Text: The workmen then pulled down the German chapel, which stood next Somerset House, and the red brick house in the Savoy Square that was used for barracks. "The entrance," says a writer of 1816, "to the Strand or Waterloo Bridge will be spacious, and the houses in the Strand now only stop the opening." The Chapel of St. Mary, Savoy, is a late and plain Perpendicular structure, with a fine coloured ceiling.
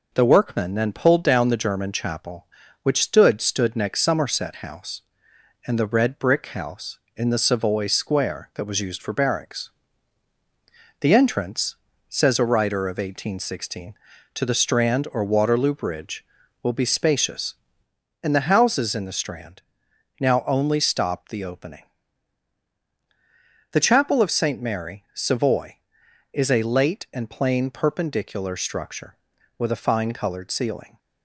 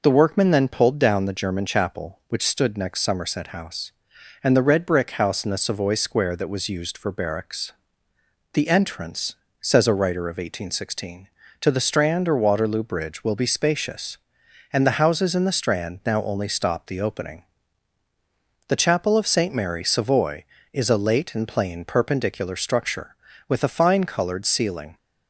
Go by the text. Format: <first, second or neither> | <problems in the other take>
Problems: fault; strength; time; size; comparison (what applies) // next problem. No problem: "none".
second | says "stood" twice; at 3.4 s // pauses between "Strand" and "now"; noticeable; at 19.6 s; 0.58 s long